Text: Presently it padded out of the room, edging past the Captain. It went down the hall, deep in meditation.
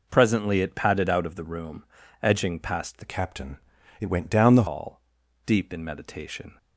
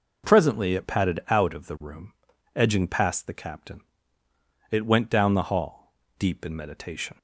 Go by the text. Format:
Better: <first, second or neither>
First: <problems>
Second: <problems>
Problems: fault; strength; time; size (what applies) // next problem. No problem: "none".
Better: second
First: changes voice from "Captain" to "the"; from 3.0 to 4.6 s; 1.6 s long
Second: none